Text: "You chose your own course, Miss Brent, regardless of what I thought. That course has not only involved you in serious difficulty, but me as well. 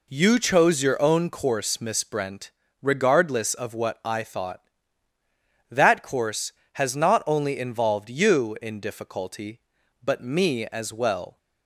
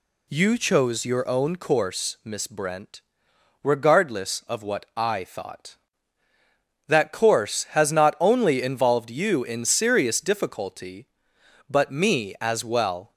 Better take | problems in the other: second | skips "serious"; at 8.7 s

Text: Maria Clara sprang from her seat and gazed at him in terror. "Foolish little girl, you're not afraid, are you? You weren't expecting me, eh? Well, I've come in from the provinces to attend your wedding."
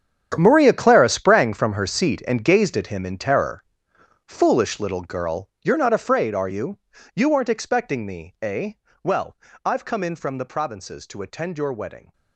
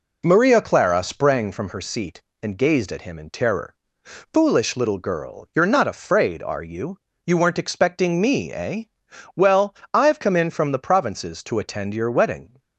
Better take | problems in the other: second | gets quieter; strong; throughout; 15 dB

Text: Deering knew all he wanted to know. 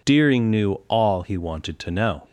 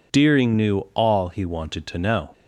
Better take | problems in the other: neither | pauses between "knew" and "all"; slight; the same in both

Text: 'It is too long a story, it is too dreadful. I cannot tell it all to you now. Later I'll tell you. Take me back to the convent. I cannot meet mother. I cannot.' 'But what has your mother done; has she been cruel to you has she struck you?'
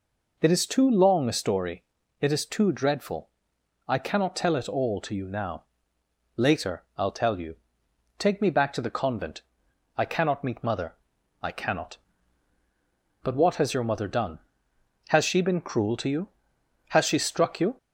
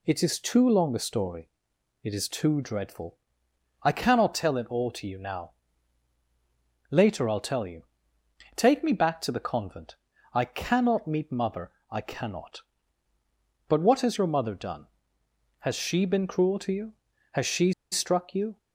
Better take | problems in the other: first | pauses between "she" and "struck"; slight; at 17.7 s; 0.20 s long

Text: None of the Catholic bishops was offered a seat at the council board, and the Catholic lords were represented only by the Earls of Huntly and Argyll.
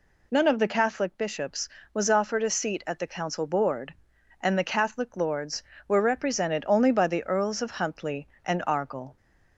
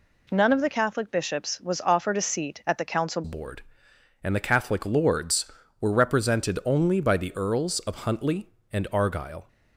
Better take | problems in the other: first | changes voice at "board"; from 3.2 s on; 6.2 s long

